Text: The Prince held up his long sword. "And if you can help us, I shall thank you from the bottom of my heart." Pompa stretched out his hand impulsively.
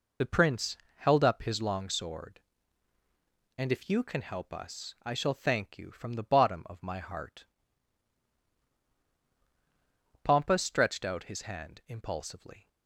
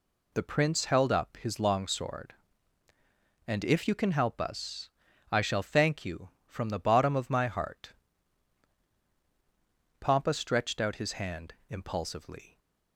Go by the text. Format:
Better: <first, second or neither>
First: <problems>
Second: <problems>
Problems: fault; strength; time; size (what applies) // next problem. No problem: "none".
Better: second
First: loses the start of "The"; at 0.2 s; 45 ms // pauses between "Prince" and "held"; slight; at 0.7 s; 0.20 s long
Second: none